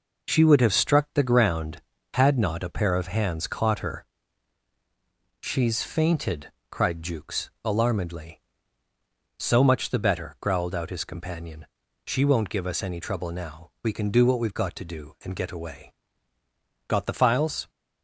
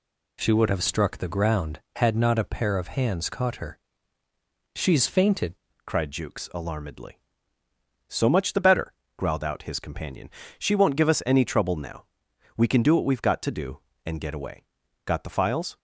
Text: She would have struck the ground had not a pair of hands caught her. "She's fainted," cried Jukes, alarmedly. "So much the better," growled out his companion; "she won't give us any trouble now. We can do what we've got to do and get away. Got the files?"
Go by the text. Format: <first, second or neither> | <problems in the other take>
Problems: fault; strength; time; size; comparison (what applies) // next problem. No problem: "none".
first | changes voice at "cried"; from 5.8 s on; 9.9 s long